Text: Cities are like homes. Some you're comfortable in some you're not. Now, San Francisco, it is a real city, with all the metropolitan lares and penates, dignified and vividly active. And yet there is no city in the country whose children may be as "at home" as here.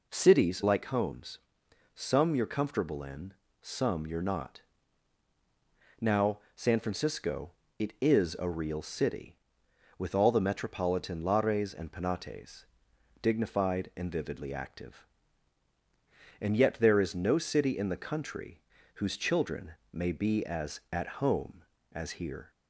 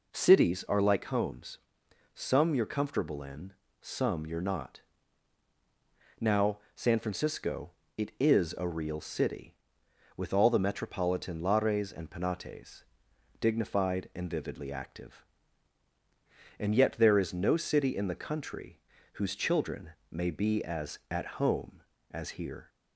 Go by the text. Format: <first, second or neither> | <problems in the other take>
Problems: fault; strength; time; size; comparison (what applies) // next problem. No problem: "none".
second | skips "are"; at 0.6 s // pauses between "in" and "some"; slight; at 3.3 s; 0.30 s long; slight in the second // pauses between "country" and "whose"; slight; at 18.6 s; 0.32 s long; slight in the second // pauses between "children" and "may"; slight; at 19.7 s; 0.20 s long; slight in the second